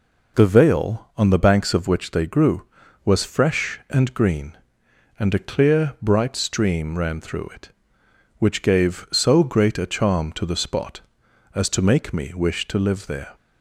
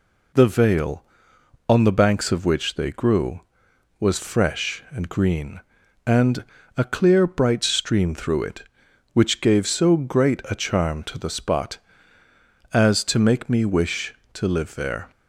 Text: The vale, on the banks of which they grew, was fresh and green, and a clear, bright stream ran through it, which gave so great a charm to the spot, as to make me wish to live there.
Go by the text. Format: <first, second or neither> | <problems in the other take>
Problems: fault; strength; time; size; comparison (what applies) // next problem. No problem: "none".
first | pauses between "and" and "a"; slight; at 6.4 s; 0.32 s long // skips "ran"; at 8.1 s